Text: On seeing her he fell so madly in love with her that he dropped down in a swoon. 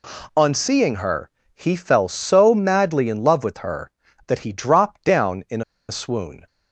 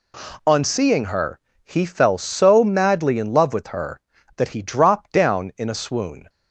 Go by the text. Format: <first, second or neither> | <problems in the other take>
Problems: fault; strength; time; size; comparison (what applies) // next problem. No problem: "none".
second | pauses between "her" and "he"; slight; at 1.3 s; 0.24 s long; slight in the second // pauses between "in" and "a"; slight; at 5.6 s; 0.25 s long